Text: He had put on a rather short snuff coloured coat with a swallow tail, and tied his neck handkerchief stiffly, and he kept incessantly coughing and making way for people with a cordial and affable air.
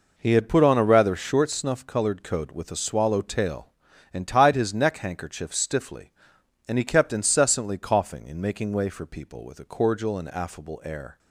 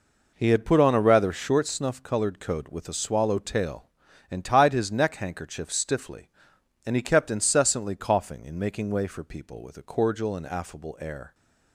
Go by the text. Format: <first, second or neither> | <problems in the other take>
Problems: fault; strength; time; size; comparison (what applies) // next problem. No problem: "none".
neither | none